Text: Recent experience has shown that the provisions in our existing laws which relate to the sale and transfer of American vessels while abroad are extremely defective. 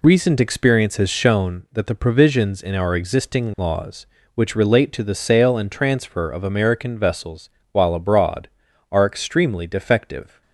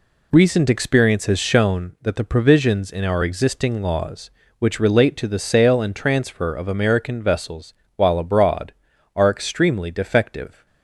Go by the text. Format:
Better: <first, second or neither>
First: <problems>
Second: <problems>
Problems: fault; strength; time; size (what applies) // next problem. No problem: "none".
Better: neither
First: pauses between "vessels" and "while"; slight; at 7.4 s; 0.22 s long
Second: pauses between "vessels" and "while"; slight; at 7.7 s; 0.22 s long